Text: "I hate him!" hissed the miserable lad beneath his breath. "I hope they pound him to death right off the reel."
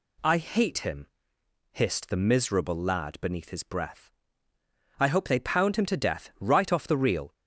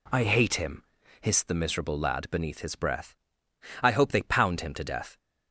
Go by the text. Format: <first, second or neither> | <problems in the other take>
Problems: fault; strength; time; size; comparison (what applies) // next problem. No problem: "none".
first | stops before "right off the reel"; at 5.1 s